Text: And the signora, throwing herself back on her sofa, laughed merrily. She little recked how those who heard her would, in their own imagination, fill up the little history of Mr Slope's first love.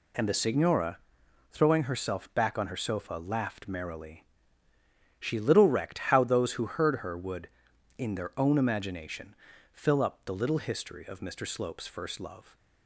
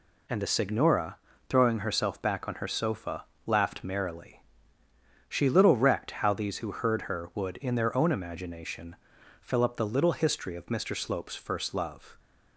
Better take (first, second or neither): first